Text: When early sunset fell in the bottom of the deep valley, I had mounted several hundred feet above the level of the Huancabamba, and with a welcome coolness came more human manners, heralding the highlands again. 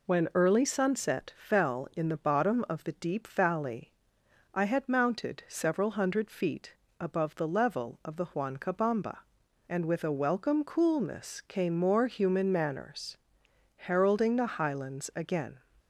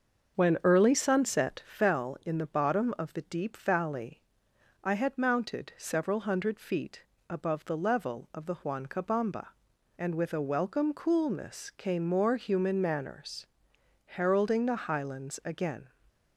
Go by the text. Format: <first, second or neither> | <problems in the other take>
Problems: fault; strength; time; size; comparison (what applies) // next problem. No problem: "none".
first | starts louder than the rest; until 1.9 s; 6.5 dB // pauses between "feet" and "above"; slight; at 7.0 s; 0.26 s long; slight in the first